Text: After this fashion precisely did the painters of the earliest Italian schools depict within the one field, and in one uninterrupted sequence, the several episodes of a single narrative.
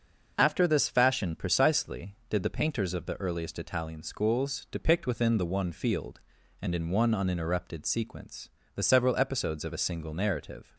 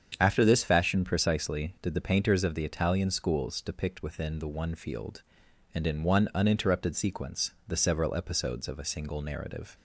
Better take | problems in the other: first | starts louder than the rest; strong; until 1.2 s; 8 dB; noticeable in the first // skips "earliest"; at 2.6 s

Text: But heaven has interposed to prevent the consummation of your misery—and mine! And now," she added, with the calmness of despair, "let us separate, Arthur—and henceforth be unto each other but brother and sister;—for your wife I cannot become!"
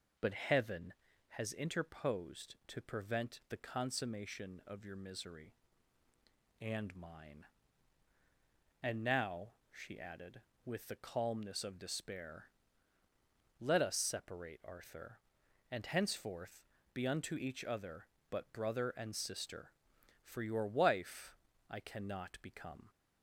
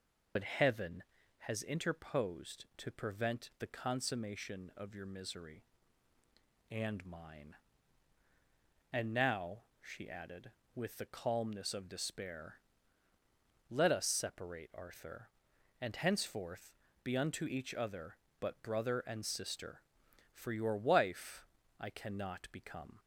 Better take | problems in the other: first | loses the start of "But"; at 0.3 s; 60 ms // pauses between "henceforth" and "be"; slight; at 16.7 s; 0.32 s long; slight in the first // pauses between "wife" and "I"; slight; at 21.4 s; 0.32 s long; slight in the first

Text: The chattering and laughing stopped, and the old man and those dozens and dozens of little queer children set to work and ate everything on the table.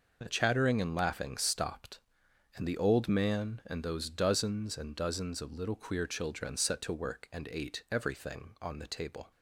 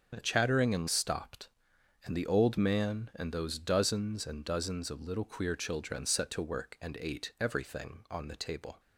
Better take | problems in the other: first | starts louder than the rest; noticeable; until 1.1 s; 6 dB // skips "laughing"; at 0.8 s

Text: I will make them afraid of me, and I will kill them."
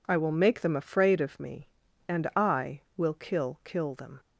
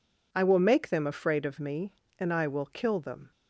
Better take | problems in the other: second | says "kill" twice; at 3.6 s

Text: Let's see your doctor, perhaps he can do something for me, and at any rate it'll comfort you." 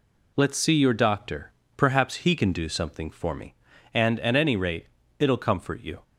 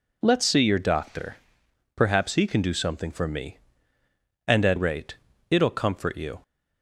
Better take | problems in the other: first | skips "any"; at 4.7 s // pauses between "rate" and "it'll"; slight; at 5.1 s; 0.34 s long; slight in the first

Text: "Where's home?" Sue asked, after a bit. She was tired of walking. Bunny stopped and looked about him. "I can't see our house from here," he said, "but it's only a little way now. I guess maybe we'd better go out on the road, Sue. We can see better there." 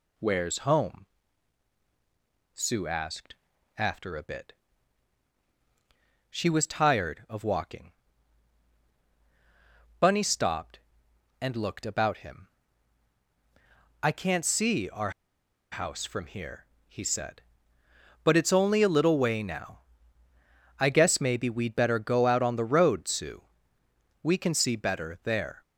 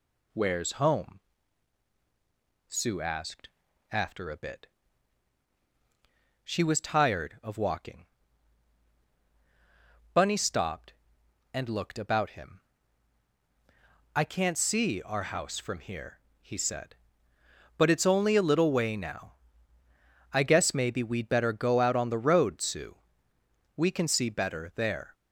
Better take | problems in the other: second | pauses between "our" and "house"; noticeable; at 15.1 s; 0.61 s long

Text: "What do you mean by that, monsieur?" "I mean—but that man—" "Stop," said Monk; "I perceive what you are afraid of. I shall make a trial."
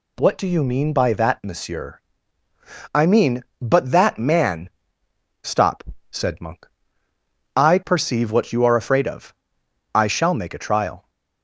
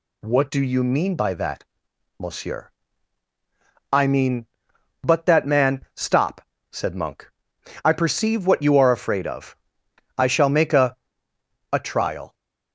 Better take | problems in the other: first | says "a" twice; at 11.7 s

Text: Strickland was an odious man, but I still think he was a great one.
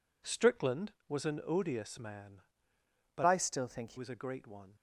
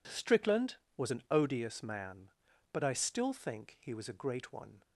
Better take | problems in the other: second | changes voice from "I" to "he"; from 3.2 to 3.9 s; 0.7 s long

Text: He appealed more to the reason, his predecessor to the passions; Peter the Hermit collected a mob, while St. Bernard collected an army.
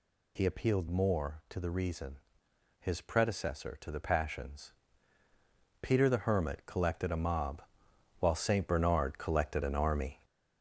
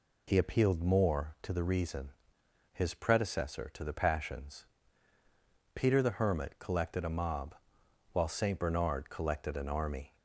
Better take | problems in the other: second | gets louder; noticeable; throughout; 4.5 dB

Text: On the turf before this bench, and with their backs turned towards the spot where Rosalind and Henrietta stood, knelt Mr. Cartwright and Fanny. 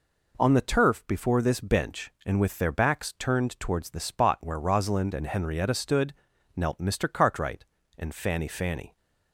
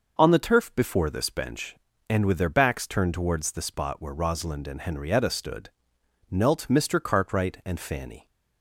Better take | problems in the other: second | says "Fanny" twice; at 8.4 s

